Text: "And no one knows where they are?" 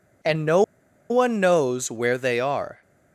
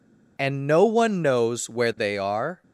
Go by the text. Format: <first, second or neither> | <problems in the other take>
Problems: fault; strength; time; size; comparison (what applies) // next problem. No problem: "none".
second | pauses between "no" and "one"; noticeable; at 0.6 s; 0.48 s long